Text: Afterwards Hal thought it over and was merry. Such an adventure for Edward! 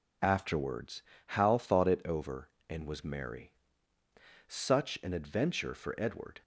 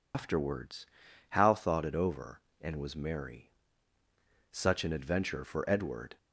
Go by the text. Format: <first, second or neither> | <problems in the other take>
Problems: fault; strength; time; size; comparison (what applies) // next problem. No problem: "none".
first | loses the start of "Afterwards"; at 0.1 s; 95 ms // pauses between "Afterwards" and "Hal"; at 0.8 s; 0.44 s long; slight in the first